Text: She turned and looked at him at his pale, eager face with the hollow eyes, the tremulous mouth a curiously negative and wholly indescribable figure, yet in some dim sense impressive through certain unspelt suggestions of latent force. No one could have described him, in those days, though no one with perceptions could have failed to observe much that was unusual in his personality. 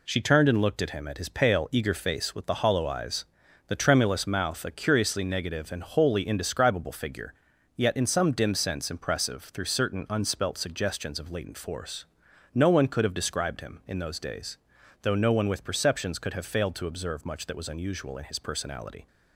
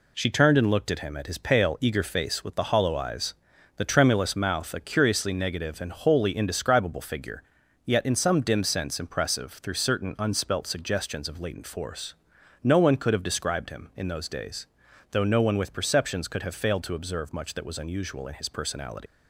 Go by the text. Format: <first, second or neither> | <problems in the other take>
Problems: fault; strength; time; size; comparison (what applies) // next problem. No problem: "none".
first | leaves "personality" unfinished; at 19.0 s; 105 ms